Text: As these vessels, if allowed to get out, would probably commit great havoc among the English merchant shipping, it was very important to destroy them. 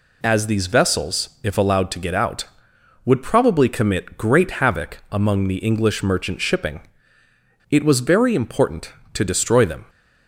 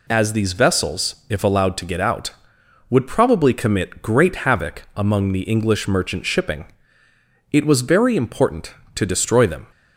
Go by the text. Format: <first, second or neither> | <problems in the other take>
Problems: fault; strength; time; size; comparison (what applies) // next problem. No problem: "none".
neither | none